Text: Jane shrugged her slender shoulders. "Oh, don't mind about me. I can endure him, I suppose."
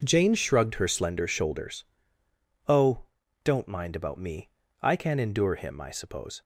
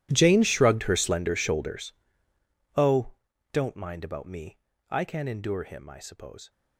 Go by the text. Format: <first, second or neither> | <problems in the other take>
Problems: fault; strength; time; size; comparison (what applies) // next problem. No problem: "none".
first | gets quieter; strong; throughout; 21.5 dB